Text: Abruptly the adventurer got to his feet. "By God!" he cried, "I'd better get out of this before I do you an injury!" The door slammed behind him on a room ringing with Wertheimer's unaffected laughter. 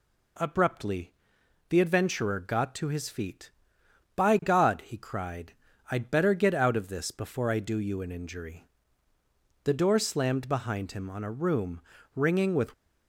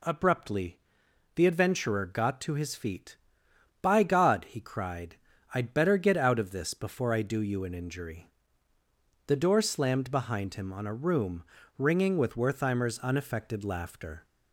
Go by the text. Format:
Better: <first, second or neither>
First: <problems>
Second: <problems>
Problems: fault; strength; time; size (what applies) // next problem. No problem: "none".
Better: second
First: pauses between "Abruptly" and "the"; noticeable; at 1.1 s; 0.58 s long // pauses between "room" and "ringing"; slight; at 11.8 s; 0.34 s long // stops before "Wertheimer's unaffected laughter"; at 12.7 s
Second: pauses between "Abruptly" and "the"; noticeable; at 0.7 s; 0.58 s long // pauses between "room" and "ringing"; slight; at 11.4 s; 0.34 s long